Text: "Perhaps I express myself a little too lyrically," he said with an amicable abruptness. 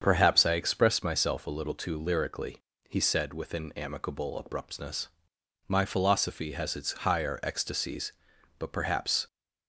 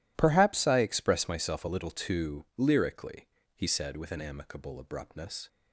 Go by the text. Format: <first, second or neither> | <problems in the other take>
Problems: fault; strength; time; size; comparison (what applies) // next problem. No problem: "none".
second | starts louder than the rest; strong; until 1.0 s; 7 dB // goes on to say "My philosophy has its higher ecstasies but perhaps"; strong; from 5.6 s on; 3.5 s long